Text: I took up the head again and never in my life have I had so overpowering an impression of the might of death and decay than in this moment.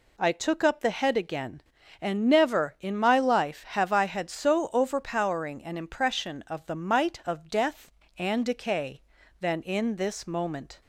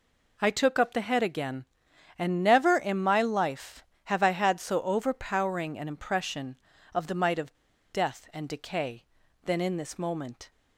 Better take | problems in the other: first | pauses between "of" and "death"; at 7.5 s; 0.36 s long

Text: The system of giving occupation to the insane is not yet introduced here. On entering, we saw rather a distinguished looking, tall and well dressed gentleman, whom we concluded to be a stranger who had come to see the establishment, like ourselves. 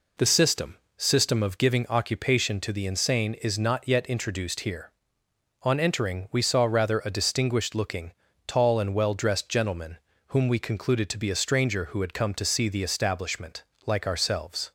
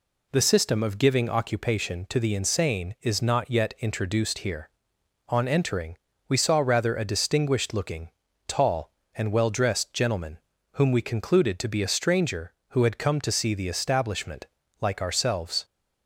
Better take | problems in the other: second | says "system" twice; at 0.9 s

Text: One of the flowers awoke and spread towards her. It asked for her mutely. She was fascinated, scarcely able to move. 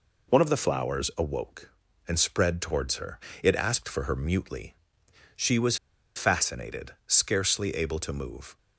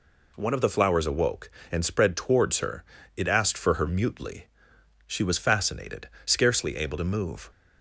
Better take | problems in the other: second | pauses between "was" and "fascinated"; at 5.7 s; 0.40 s long

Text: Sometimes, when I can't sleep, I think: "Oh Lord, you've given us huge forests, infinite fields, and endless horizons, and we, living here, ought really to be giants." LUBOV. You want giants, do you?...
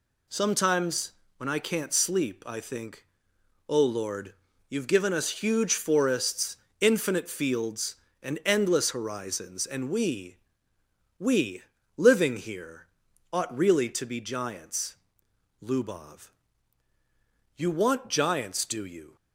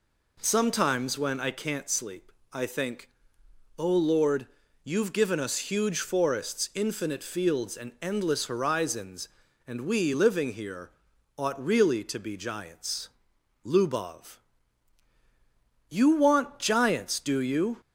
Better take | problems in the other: second | says "we" twice; at 11.1 s

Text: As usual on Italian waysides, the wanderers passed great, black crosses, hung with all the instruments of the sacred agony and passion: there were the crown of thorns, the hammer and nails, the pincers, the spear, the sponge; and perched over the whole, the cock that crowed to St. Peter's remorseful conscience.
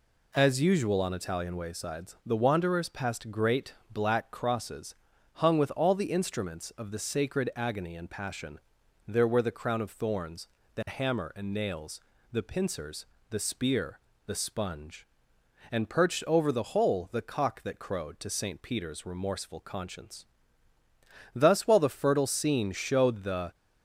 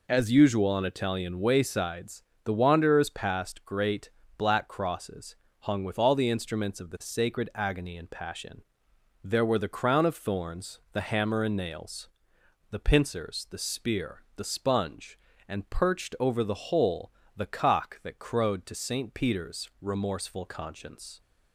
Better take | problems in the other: second | goes on to say "Thus while the fertile scene showed the"; strong; from 21.3 s on; 2.2 s long

